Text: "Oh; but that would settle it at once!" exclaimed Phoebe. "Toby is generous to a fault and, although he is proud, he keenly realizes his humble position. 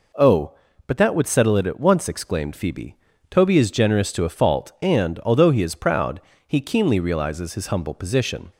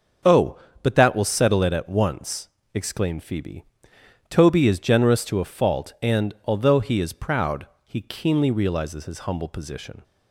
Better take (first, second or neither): first